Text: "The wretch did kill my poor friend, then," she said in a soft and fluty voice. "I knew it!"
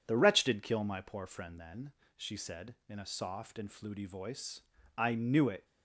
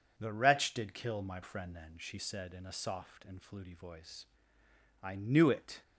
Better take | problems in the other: first | skips "poor"; at 1.4 s

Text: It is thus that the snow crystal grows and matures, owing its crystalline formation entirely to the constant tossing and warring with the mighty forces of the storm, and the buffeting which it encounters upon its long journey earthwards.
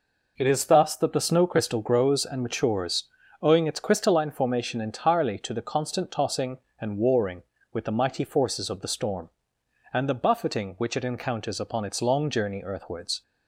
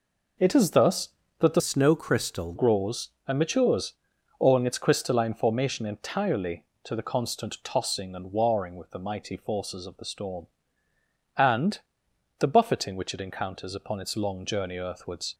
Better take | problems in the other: first | changes voice from "snow" to "crystal"; from 1.5 to 2.5 s; 1.0 s long // pauses between "and" and "the"; noticeable; at 11.8 s; 0.58 s long

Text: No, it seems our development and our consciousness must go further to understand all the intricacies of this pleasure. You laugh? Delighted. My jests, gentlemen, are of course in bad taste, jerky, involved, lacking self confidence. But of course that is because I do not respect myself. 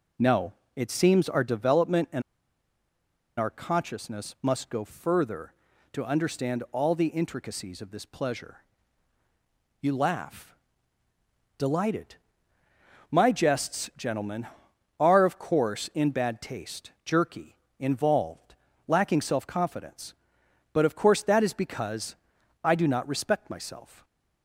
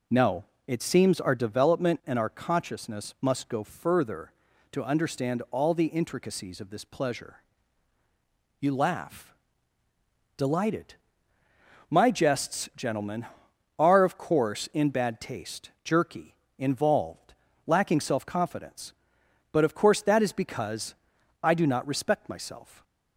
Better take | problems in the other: second | pauses between "and" and "our"; at 2.2 s; 1.1 s long // pauses between "because" and "I"; noticeable; at 22.1 s; 0.48 s long; noticeable in the second

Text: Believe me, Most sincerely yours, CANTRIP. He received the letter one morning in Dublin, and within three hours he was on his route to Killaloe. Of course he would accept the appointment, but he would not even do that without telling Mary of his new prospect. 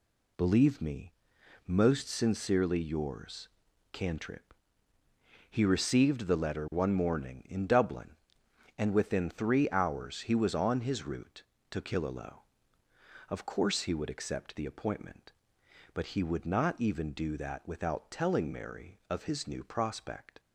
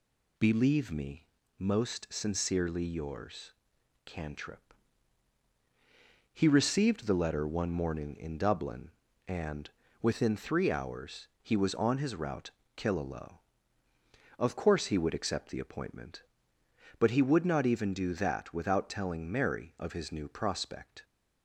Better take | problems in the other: first | pauses between "and" and "within"; slight; at 9.7 s; 0.32 s long // skips "to"; at 12.6 s

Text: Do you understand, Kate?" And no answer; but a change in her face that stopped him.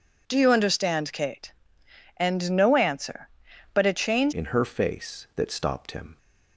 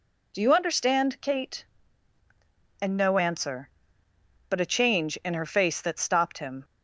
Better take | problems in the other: second | changes voice at "in"; from 4.3 s on; 1.8 s long

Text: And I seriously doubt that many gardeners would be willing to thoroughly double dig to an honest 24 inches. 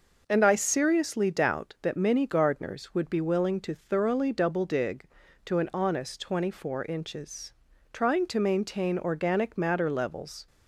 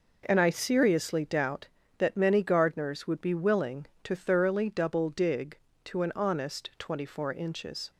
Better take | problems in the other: second | goes on to say "Trying to maintain organic matter levels"; strong; from 7.9 s on; 2.5 s long

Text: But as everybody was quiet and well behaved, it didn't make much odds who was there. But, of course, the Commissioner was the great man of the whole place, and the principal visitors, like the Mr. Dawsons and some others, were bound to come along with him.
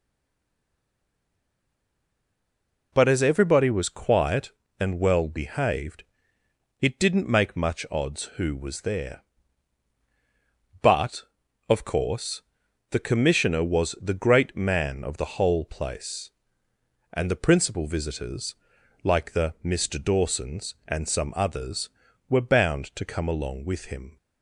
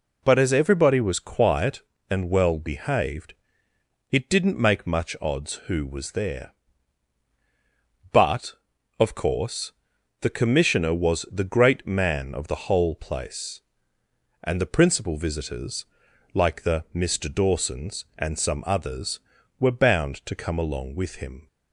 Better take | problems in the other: second | stays silent before the first word; strong; until 2.9 s; 2.9 s long

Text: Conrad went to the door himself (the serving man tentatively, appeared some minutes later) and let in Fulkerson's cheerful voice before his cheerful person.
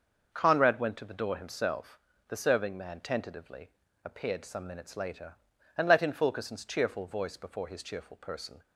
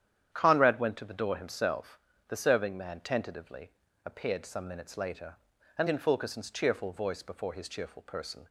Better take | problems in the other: first | starts louder than the rest; strong; until 1.3 s; 10 dB; also in the first // skips "let"; at 5.8 s

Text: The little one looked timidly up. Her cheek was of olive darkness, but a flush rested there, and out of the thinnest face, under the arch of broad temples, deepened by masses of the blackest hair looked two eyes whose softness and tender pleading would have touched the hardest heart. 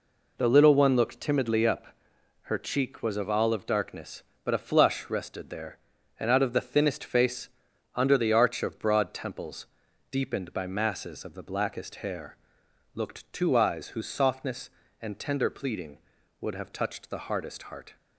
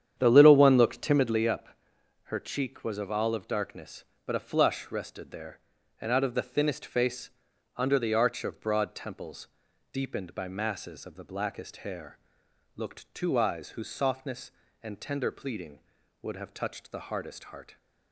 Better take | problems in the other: first | starts louder than the rest; strong; until 1.5 s; 9 dB // pauses between "hair" and "looked"; noticeable; at 12.1 s; 0.58 s long; noticeable in the first

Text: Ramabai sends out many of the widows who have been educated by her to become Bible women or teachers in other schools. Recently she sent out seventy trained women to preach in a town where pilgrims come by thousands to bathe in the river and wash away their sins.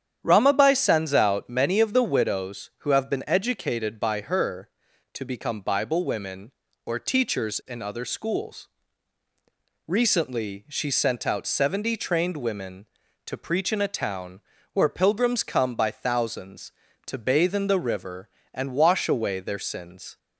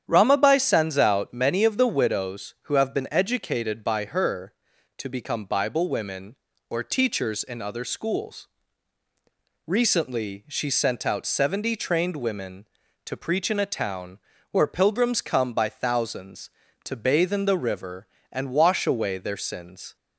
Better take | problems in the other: neither | starts louder than the rest; strong; the same in both // pauses between "town" and "where"; slight; the same in both

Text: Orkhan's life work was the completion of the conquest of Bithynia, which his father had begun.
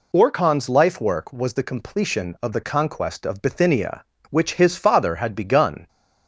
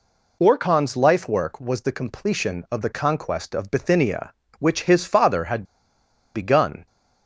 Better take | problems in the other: first | pauses between "had" and "begun"; noticeable; at 5.6 s; 0.72 s long

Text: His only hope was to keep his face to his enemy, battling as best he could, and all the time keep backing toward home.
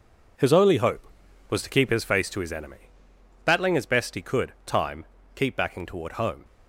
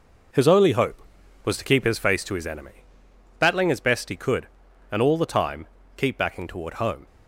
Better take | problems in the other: second | skips "and all the"; at 4.5 s // pauses between "time" and "keep"; slight; at 5.0 s; 0.32 s long; slight in the second

